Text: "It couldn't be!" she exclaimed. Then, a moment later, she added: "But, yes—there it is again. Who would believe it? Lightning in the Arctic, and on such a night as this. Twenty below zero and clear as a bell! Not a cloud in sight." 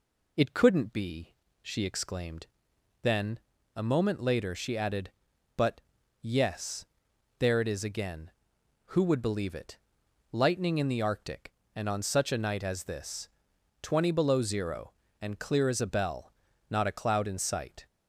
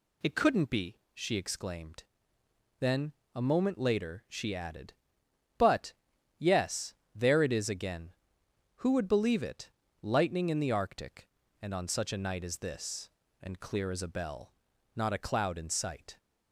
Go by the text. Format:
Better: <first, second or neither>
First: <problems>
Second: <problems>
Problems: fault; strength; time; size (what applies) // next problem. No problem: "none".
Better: first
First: none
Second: skips "Twenty below zero"; at 13.2 s